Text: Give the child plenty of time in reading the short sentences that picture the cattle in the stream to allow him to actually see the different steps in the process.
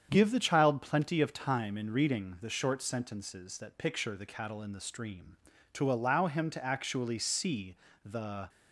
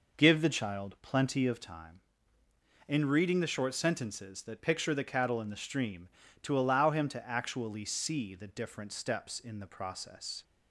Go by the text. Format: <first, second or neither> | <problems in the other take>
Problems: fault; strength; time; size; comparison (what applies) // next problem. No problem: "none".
second | starts louder than the rest; strong; until 1.1 s; 8 dB // pauses between "see" and "the"; slight; at 7.7 s; 0.28 s long // stops before "different steps in the process"; at 8.4 s